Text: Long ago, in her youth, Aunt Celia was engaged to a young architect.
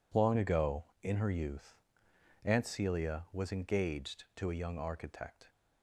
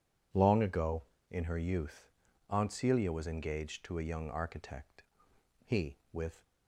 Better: first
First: none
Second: goes on to say "He with"; noticeable; from 5.6 s on; 0.80 s long

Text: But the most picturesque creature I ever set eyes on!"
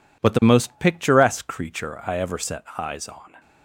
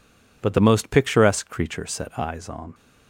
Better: first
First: none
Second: skips "I ever"; at 1.8 s

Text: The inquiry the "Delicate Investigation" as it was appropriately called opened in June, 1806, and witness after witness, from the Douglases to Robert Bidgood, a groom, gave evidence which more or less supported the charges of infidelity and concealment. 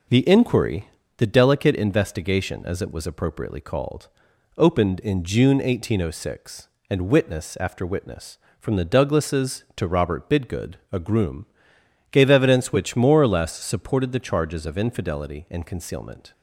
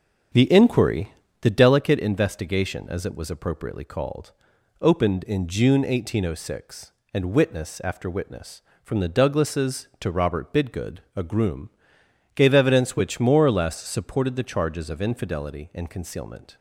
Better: first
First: pauses between "inquiry" and "the"; slight; at 0.8 s; 0.30 s long // pauses between "called" and "opened"; noticeable; at 4.0 s; 0.48 s long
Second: starts louder than the rest; until 1.8 s; 7 dB // pauses between "inquiry" and "the"; slight; at 1.1 s; 0.30 s long // pauses between "called" and "opened"; noticeable; at 4.3 s; 0.48 s long

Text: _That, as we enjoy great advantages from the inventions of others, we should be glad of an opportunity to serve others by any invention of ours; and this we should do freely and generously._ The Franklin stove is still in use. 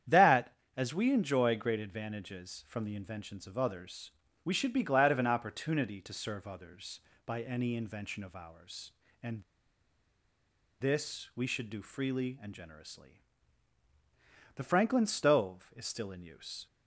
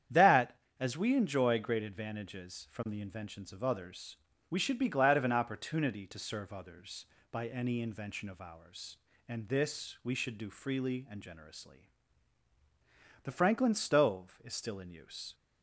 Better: second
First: starts louder than the rest; strong; until 1.2 s; 9 dB // pauses between "and" and "this"; strong; at 9.4 s; 1.3 s long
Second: starts louder than the rest; strong; until 1.3 s; 9 dB

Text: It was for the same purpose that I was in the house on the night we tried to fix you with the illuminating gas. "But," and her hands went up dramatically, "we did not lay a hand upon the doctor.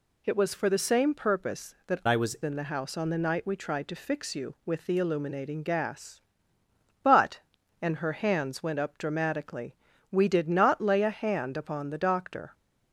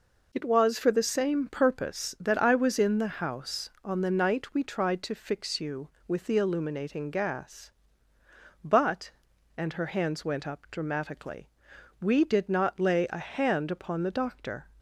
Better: second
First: changes voice from "I" to "was"; from 2.0 to 2.3 s; 0.3 s long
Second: none

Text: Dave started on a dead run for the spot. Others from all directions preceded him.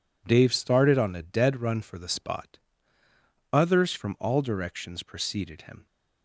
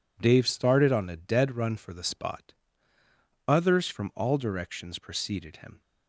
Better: neither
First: none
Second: none

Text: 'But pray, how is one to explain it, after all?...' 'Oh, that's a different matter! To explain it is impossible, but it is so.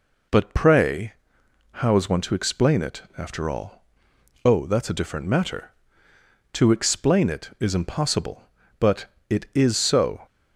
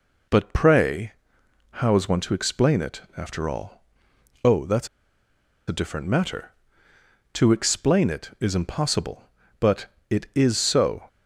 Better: first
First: pauses between "but" and "it"; slight; at 9.0 s; 0.24 s long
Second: pauses between "that's" and "a"; noticeable; at 4.8 s; 0.81 s long // pauses between "but" and "it"; slight; at 9.8 s; 0.24 s long

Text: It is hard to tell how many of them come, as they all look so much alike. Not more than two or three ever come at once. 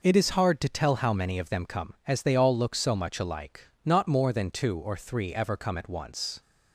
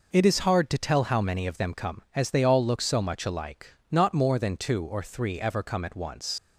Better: first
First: none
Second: leaves "once" unfinished; at 6.3 s; 95 ms

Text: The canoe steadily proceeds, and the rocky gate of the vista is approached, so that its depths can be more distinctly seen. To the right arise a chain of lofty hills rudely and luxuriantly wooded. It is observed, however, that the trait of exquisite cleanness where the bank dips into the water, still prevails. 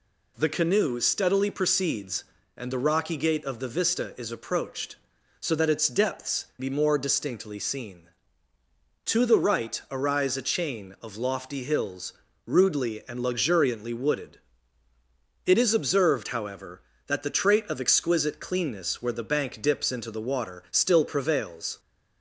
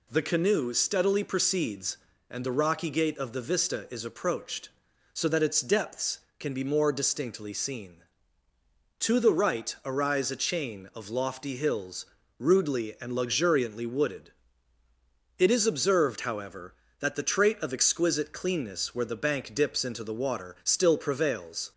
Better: second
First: skips "can"; at 6.5 s // pauses between "hills" and "rudely"; slight; at 12.1 s; 0.32 s long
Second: pauses between "hills" and "rudely"; slight; at 12.0 s; 0.32 s long

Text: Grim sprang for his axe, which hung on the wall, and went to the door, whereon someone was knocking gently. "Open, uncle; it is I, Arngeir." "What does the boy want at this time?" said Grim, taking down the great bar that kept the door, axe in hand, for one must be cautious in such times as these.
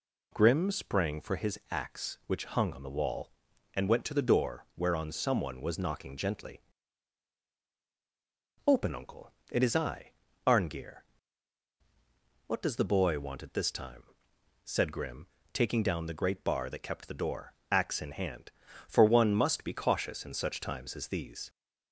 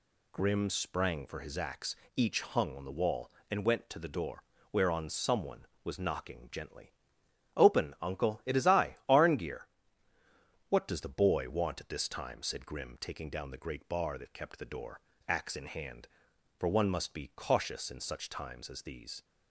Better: first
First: none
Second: says "each" for "which"; at 2.1 s

